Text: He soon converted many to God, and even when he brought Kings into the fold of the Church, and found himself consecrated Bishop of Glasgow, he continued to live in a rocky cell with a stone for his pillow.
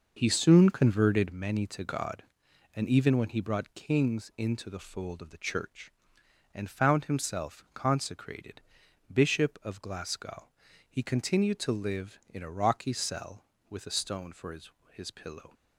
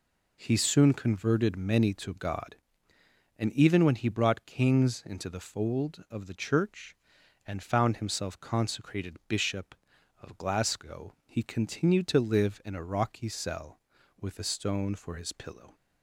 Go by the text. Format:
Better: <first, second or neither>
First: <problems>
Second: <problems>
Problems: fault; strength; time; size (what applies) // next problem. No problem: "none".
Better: second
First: pauses between "consecrated" and "Bishop"; noticeable; at 8.5 s; 0.54 s long // says "his" twice; at 14.9 s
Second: none